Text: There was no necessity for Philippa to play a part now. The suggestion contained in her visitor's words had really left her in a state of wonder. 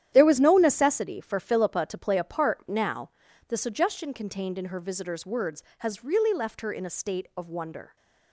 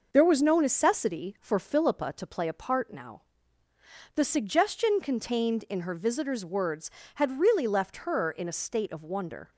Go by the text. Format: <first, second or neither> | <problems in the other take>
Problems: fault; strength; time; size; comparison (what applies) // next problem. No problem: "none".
second | starts louder than the rest; strong; until 1.1 s; 11 dB // says "has" for "had"; at 5.7 s